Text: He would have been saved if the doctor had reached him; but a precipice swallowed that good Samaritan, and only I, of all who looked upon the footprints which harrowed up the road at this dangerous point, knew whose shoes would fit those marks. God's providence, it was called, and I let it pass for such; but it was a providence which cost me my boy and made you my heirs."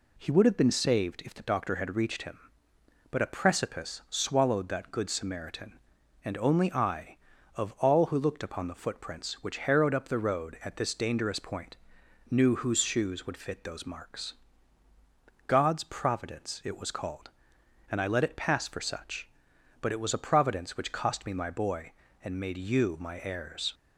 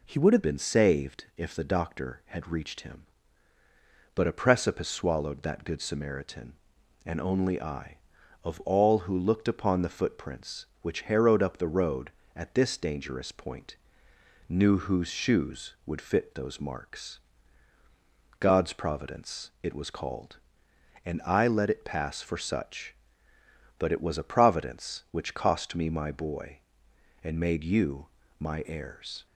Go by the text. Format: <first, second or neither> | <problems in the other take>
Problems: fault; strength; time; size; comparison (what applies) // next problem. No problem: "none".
first | changes voice at "been"; from 0.4 s on; 28.8 s long // pauses between "you" and "my"; slight; at 28.0 s; 0.32 s long